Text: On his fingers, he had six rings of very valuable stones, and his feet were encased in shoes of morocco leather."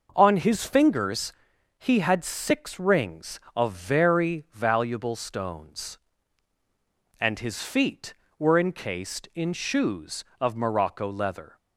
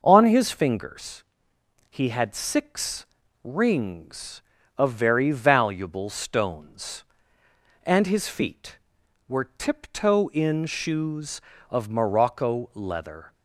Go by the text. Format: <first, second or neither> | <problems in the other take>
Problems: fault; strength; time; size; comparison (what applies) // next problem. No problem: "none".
first | pauses between "six" and "rings"; at 3.0 s; 0.38 s long // says "tiptoe" for "encased"; at 9.5 s